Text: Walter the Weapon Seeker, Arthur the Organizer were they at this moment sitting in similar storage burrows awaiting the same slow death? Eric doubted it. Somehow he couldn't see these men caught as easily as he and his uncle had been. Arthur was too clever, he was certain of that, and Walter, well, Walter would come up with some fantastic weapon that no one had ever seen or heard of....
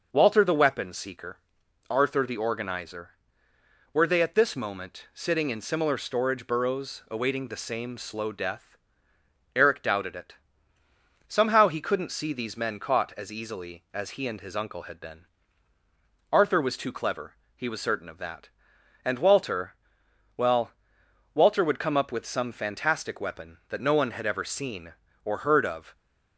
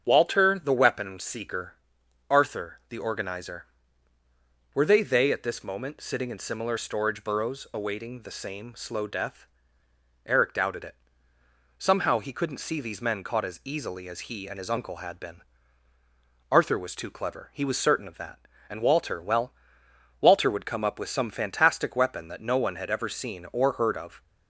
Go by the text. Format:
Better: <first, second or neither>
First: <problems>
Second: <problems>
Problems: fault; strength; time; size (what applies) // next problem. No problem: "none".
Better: first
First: starts louder than the rest; noticeable; until 1.1 s; 6 dB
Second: starts louder than the rest; strong; until 1.0 s; 7 dB // says "they" twice; at 5.0 s